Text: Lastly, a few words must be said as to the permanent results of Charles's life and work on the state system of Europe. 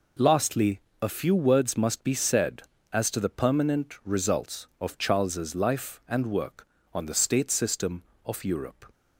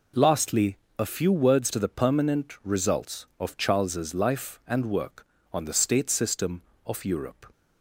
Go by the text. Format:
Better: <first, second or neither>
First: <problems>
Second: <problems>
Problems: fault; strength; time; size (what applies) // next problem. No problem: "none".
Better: first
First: none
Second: skips "must be said as"; at 1.7 s